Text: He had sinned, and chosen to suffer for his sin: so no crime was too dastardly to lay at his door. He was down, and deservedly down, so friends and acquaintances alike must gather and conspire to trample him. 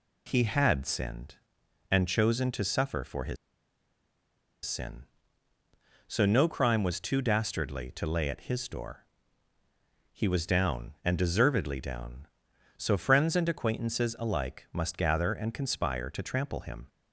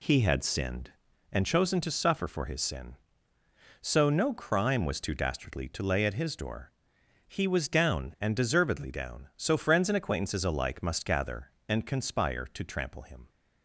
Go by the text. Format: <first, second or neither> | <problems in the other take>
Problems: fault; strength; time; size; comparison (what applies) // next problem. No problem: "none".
second | pauses between "his" and "sin"; strong; at 3.3 s; 1.2 s long